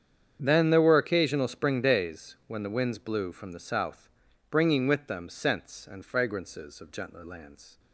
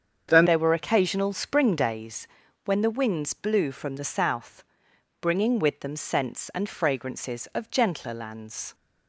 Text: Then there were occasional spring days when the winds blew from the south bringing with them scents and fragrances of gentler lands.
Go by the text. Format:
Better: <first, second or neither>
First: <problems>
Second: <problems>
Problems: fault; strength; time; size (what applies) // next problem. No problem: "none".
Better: first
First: starts louder than the rest; strong; until 1.4 s; 8 dB // pauses between "south" and "bringing"; at 4.0 s; 0.40 s long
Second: starts louder than the rest; strong; until 1.3 s; 7.5 dB // changes voice at "there"; from 0.4 s on; 8.3 s long // pauses between "days" and "when"; slight; at 2.2 s; 0.36 s long // pauses between "south" and "bringing"; noticeable; at 4.6 s; 0.58 s long